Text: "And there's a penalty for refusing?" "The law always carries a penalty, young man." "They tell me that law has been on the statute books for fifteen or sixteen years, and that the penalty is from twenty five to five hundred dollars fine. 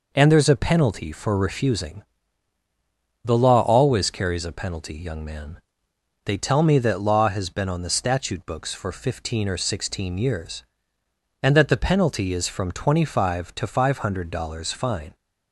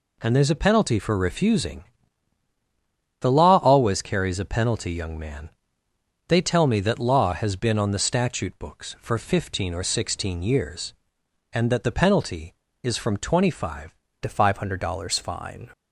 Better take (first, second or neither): first